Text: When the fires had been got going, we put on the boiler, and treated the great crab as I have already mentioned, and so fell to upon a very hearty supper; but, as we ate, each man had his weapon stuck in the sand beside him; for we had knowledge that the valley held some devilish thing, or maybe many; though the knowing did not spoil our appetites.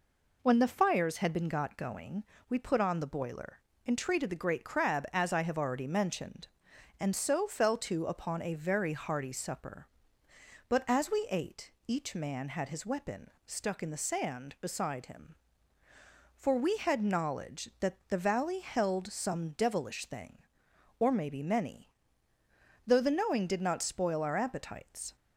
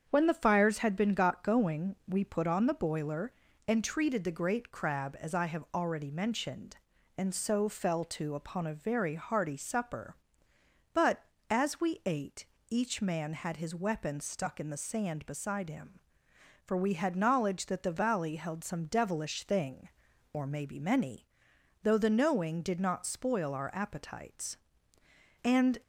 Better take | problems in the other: first | starts louder than the rest; strong; until 1.1 s; 7.5 dB // goes on to say "And"; slight; from 25.4 s on; 0.36 s long

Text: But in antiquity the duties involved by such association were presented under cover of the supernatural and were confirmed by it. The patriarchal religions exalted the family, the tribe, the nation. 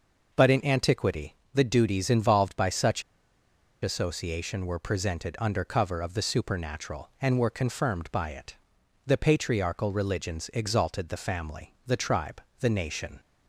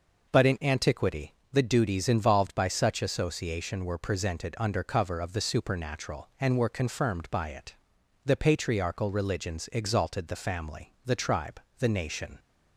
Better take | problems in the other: second | pauses between "antiquity" and "the"; slight; at 1.3 s; 0.20 s long; slight in the second // pauses between "such" and "association"; noticeable; at 3.0 s; 0.81 s long

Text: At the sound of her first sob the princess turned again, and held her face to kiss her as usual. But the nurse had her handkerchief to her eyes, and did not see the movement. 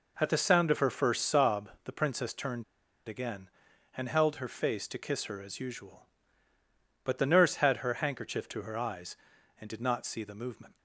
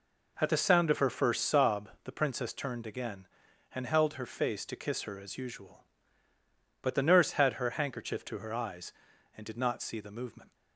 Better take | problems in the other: second | pauses between "turned" and "again"; at 2.6 s; 0.43 s long

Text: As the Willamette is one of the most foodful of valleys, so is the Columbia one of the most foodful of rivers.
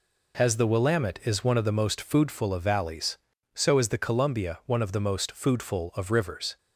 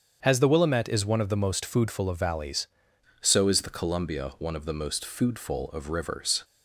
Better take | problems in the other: first | starts louder than the rest; strong; until 1.2 s; 7 dB // changes voice at "so"; from 3.2 s on; 3.2 s long

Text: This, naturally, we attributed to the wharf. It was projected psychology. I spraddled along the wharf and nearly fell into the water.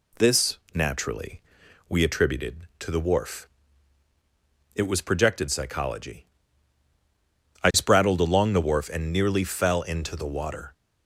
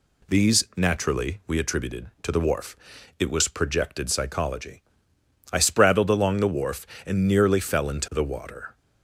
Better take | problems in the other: first | says "These" for "This"; at 0.2 s

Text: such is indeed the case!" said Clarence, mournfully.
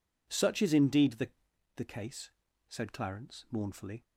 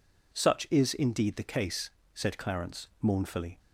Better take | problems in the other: second | says "the" twice; at 1.7 s

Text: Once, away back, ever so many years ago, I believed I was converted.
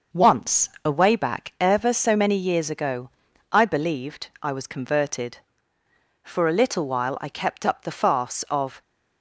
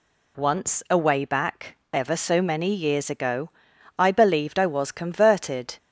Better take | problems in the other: second | pauses between "believed" and "I"; slight; at 4.2 s; 0.16 s long // goes on to say "For a little while I kept up the farce of"; strong; from 6.2 s on; 2.5 s long

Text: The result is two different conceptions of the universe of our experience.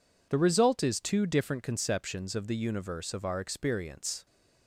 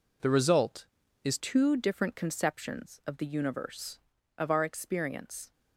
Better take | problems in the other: first | changes voice at "two"; from 1.3 s on; 4.2 s long

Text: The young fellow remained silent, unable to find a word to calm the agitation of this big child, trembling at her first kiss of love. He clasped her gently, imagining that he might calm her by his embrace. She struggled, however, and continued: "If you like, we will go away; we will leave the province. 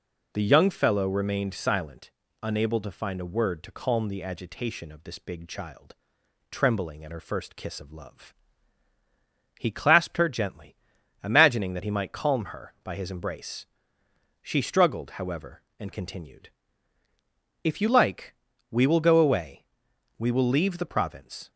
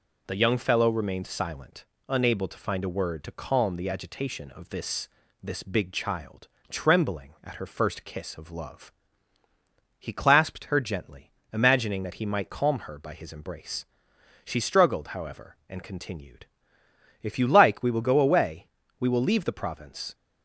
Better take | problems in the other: first | says "this" twice; at 5.4 s

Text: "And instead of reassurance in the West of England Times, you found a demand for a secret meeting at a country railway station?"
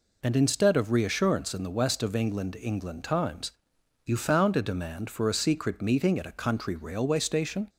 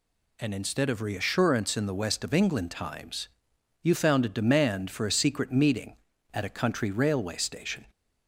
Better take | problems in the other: second | says "England" twice; at 2.5 s

